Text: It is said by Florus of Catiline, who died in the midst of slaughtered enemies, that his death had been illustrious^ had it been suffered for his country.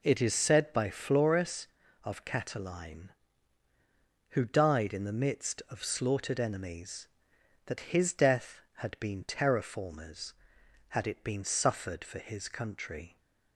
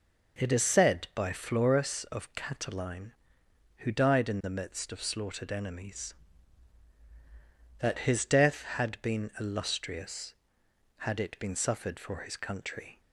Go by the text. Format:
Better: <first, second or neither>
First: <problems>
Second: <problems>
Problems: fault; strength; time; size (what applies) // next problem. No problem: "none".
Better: second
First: says "terraformers" for "illustrious"; at 9.2 s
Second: none